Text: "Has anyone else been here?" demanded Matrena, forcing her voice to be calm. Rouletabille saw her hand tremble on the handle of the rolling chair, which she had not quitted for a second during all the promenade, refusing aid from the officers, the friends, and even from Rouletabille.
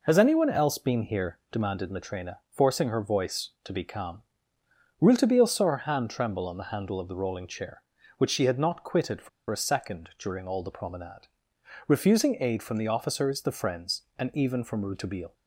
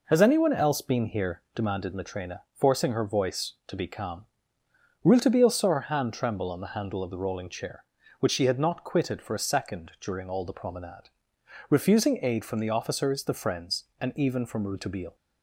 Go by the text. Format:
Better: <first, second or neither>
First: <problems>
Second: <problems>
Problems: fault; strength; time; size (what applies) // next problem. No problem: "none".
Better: second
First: pauses between "for" and "a"; slight; at 9.2 s; 0.21 s long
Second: none